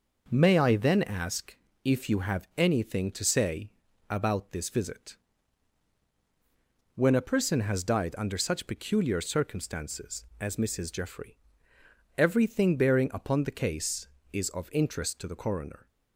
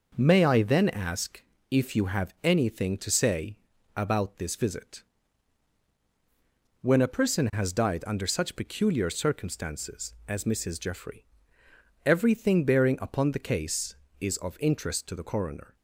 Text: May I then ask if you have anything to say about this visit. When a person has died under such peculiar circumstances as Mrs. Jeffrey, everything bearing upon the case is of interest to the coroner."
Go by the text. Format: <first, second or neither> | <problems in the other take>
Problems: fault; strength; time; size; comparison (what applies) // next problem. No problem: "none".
neither | pauses between "ask" and "if"; slight; the same in both // pauses between "say" and "about"; the same in both